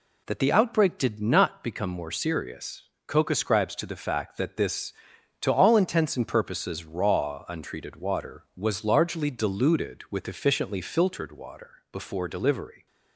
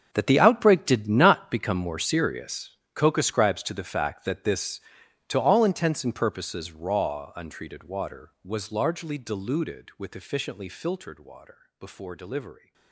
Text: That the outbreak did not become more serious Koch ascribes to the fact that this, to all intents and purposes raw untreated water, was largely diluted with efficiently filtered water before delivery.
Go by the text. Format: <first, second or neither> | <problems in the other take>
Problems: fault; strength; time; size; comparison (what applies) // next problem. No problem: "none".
first | gets quieter; strong; throughout; 16 dB // pauses between "serious" and "Koch"; slight; at 2.7 s; 0.22 s long; slight in the first